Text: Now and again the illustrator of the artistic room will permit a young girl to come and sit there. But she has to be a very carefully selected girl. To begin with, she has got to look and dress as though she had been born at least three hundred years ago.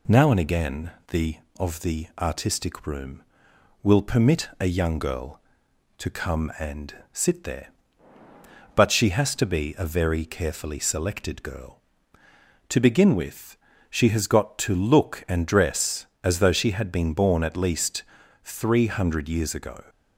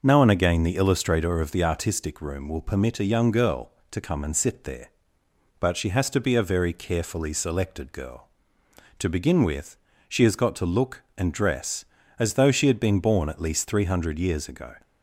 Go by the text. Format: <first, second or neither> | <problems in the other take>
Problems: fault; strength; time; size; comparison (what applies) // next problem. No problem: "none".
second | pauses between "again" and "the"; slight; at 0.9 s; 0.16 s long // skips "illustrator"; at 1.4 s // pauses between "and" and "sit"; slight; at 6.9 s; 0.18 s long // pauses between "least" and "three"; at 18.0 s; 0.40 s long